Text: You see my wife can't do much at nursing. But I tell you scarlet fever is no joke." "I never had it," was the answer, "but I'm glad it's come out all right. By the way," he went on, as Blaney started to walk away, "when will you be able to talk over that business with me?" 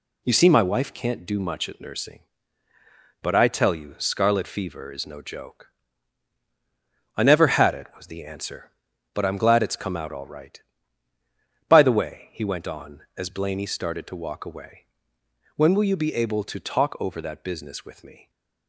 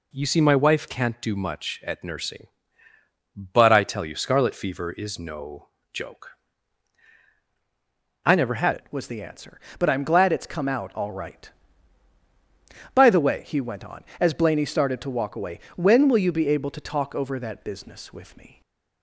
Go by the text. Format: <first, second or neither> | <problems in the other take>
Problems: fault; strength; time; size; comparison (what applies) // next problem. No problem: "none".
first | pauses between "no" and "joke"; slight; at 5.6 s; 0.26 s long // changes voice at "it"; from 8.7 s on; 9.9 s long // stays silent after the last word; slight; from 18.5 s on; 0.5 s long